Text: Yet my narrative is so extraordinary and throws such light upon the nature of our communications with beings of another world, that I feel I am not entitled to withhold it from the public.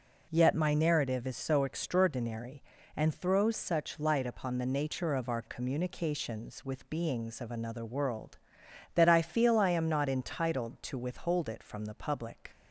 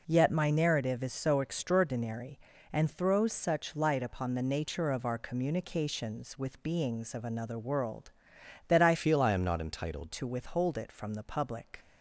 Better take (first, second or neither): first